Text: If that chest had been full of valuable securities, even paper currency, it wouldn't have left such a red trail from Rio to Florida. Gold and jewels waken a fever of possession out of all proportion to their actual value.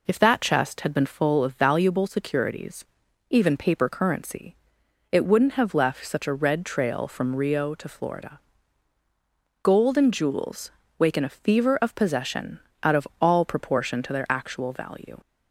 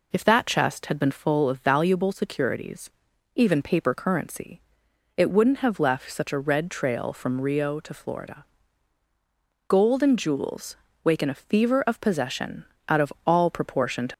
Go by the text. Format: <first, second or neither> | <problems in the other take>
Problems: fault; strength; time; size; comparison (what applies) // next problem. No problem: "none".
first | pauses between "jewels" and "waken"; slight; at 10.7 s; 0.28 s long; slight in the first // pauses between "possession" and "out"; slight; at 12.6 s; 0.24 s long; slight in the first // stops before "their actual value"; at 14.1 s